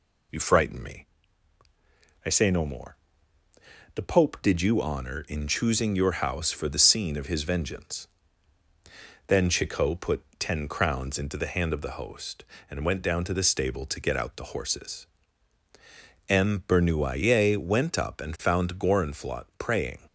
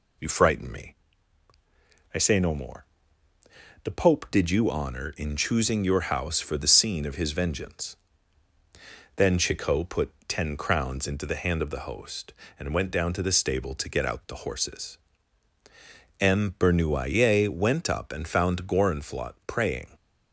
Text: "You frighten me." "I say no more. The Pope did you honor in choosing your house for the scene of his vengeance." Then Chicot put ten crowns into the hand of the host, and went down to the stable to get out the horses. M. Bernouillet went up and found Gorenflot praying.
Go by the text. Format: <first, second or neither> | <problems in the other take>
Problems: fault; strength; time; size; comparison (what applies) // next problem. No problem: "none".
neither | pauses between "put" and "ten"; slight; the same in both